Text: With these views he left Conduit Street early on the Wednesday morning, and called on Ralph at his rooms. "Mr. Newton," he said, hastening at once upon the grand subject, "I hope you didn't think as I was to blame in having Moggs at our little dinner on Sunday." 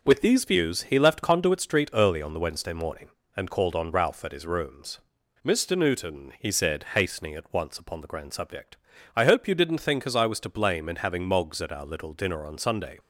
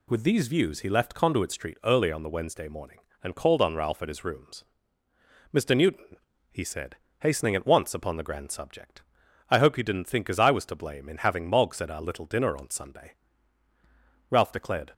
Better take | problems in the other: first | goes on to say "Ralph declared"; noticeable; from 14.3 s on; 0.62 s long

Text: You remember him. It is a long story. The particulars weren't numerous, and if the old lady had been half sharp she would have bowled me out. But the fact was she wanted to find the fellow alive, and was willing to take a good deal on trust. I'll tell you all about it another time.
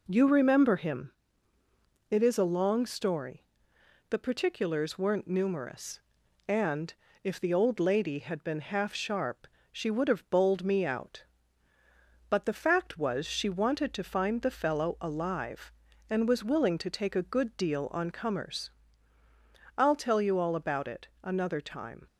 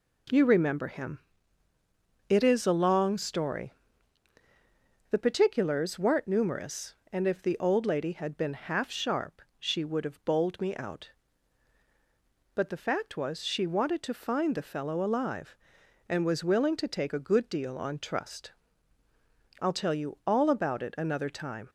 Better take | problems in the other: second | pauses between "and" and "if"; slight; at 6.9 s; 0.30 s long // pauses between "sharp" and "she"; slight; at 9.4 s; 0.24 s long; slight in the second // says "comers" for "trust"; at 18.1 s // pauses between "it" and "another"; slight; at 21.0 s; 0.16 s long

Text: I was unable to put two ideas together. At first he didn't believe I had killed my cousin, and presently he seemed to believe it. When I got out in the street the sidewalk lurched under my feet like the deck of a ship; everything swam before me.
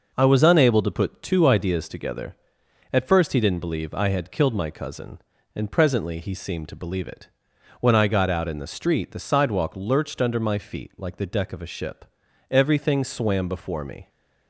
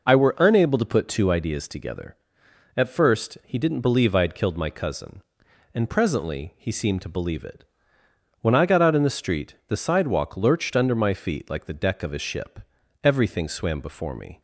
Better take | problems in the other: first | says "were" for "was"; at 0.1 s

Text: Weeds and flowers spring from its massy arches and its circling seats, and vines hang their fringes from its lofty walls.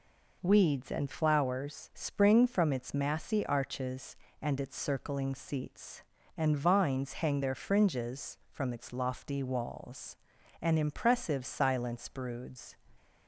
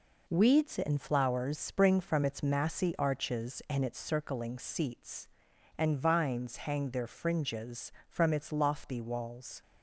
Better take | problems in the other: second | goes on to say "An impressive silence broods"; strong; from 10.6 s on; 2.1 s long

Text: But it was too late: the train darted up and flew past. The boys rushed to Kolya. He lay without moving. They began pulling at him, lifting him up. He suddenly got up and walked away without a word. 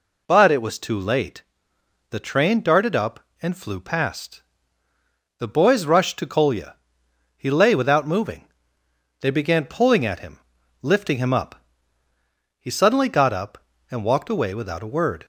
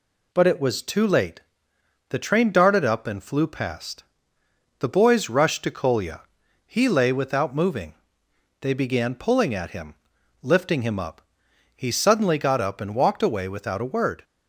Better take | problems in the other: neither | none

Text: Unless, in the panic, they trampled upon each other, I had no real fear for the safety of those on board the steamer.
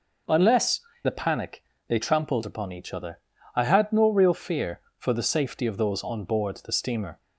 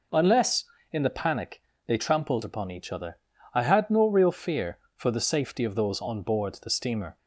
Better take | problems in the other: second | skips "in"; at 0.9 s

